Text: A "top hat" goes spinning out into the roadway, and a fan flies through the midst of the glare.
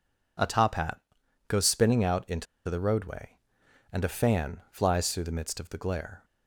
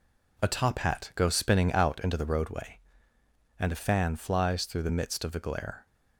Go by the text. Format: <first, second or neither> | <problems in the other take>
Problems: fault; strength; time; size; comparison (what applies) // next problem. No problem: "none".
second | pauses between "hat" and "goes"; noticeable; at 1.0 s; 0.48 s long // pauses between "into" and "the"; slight; at 2.4 s; 0.22 s long